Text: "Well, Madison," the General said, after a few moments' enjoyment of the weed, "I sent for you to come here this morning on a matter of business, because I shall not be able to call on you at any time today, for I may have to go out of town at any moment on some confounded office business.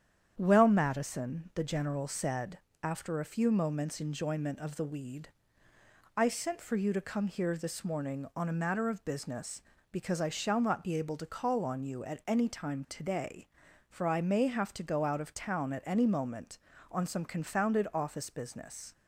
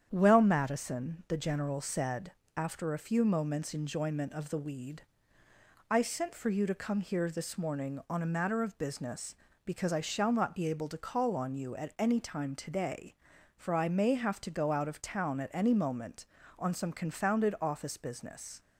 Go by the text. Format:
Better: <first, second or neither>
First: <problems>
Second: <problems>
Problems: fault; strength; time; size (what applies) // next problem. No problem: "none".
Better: neither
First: starts louder than the rest; strong; until 1.3 s; 8.5 dB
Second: starts louder than the rest; strong; until 1.1 s; 8.5 dB